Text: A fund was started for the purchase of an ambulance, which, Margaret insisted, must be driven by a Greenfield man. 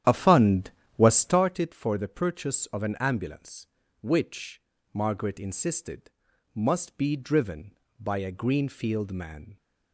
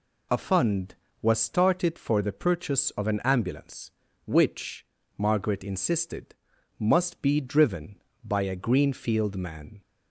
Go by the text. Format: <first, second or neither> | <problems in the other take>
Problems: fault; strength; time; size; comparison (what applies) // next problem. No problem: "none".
second | starts louder than the rest; strong; until 1.5 s; 10.5 dB